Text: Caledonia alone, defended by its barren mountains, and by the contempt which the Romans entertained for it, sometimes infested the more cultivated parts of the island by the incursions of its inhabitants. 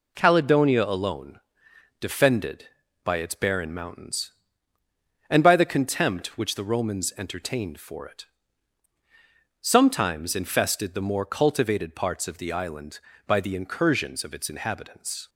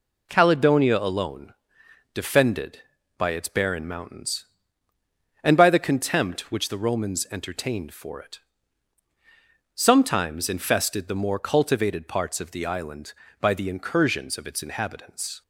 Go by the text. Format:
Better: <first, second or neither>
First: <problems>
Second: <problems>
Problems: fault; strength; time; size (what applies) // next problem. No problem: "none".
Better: neither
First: none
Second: none